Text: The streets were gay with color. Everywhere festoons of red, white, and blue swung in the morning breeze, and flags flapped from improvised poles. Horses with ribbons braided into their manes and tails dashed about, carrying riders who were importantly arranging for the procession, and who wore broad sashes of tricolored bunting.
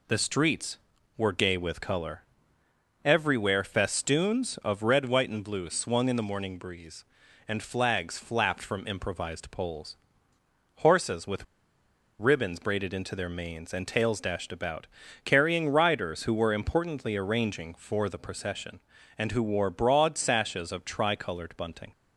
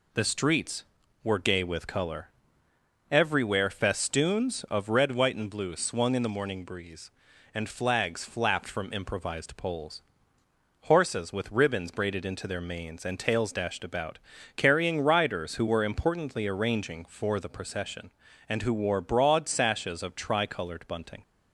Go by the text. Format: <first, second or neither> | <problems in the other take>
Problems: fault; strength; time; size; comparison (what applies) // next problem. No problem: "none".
second | pauses between "with" and "ribbons"; noticeable; at 11.4 s; 0.75 s long